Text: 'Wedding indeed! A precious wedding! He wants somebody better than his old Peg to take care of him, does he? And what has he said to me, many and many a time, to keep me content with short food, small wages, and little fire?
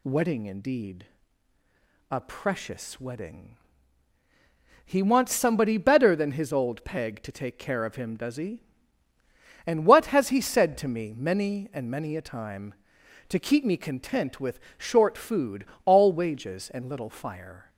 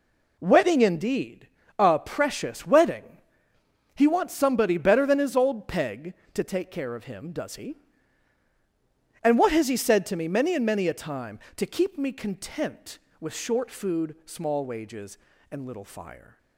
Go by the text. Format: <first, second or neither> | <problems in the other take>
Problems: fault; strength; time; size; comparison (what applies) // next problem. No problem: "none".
second | pauses between "with" and "short"; slight; at 14.5 s; 0.18 s long // says "all" for "small"; at 15.8 s